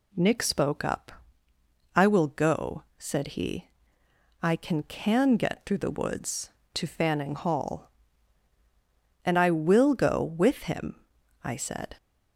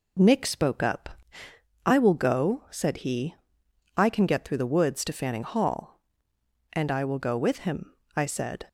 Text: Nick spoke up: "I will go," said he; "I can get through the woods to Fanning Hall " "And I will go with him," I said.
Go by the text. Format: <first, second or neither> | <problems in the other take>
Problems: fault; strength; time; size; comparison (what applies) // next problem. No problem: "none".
second | says "can" twice; at 4.8 s